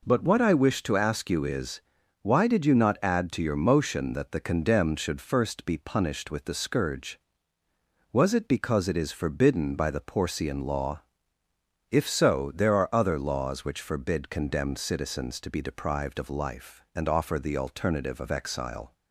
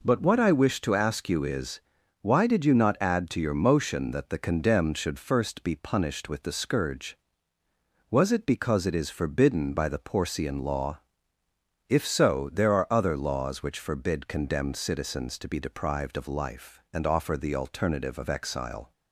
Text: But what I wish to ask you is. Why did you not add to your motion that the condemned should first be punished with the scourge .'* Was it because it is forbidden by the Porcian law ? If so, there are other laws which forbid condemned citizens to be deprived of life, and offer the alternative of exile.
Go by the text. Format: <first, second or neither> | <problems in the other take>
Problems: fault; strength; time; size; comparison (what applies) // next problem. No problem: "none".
neither | none